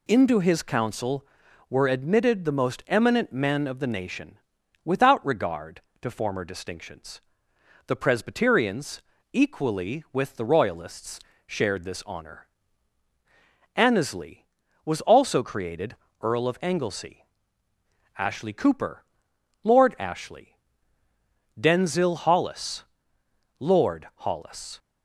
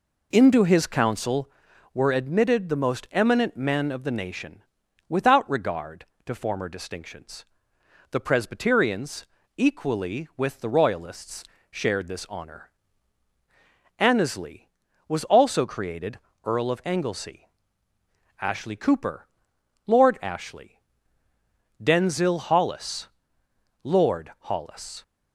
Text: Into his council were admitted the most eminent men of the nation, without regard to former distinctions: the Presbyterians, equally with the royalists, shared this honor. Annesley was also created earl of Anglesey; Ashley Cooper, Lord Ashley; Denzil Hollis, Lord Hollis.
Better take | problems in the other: first | starts louder than the rest; until 1.5 s; 4 dB // pauses between "created" and "earl"; slight; at 16.2 s; 0.24 s long; slight in the first

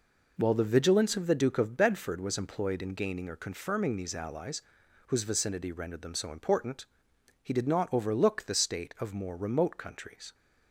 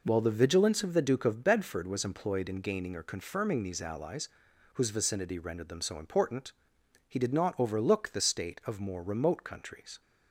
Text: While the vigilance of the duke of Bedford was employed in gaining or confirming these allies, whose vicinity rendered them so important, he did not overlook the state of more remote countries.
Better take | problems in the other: neither | none

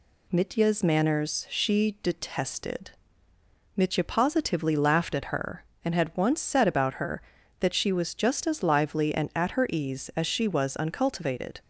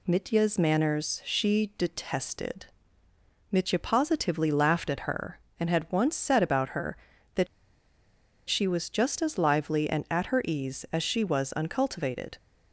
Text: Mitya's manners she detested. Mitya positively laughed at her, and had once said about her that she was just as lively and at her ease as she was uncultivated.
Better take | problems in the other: first | pauses between "that" and "she"; at 7.4 s; 1.0 s long

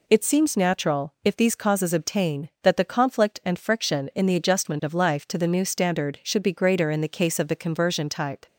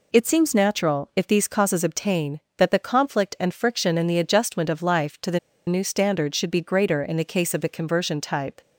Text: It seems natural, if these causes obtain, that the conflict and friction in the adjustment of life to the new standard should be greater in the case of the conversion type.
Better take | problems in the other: first | pauses between "the" and "new"; slight; at 5.3 s; 0.28 s long

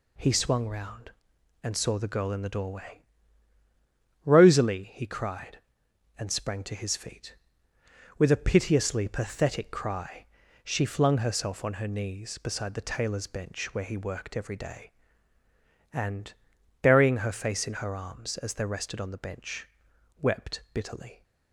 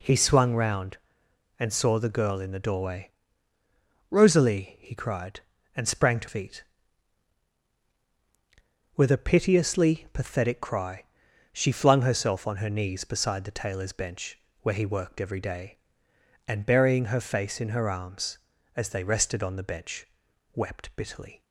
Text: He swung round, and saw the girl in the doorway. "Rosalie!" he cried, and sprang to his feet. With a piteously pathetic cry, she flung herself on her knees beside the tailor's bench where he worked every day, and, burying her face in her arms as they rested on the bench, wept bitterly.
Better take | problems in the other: first | skips "his"; at 6.2 s // pauses between "bench" and "where"; slight; at 14.3 s; 0.22 s long

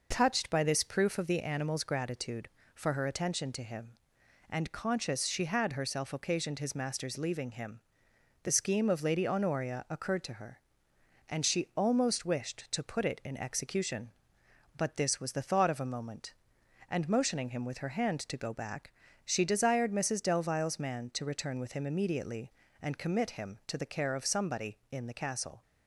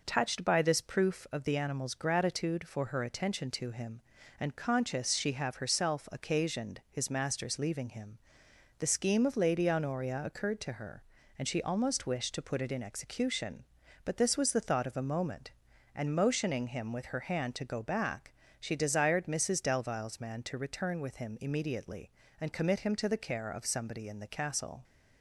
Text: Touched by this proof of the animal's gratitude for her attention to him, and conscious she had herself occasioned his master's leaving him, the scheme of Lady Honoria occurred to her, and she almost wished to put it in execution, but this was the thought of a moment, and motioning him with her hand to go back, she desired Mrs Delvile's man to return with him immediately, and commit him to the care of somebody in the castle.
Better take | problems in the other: first | says "have" for "had"; at 5.3 s

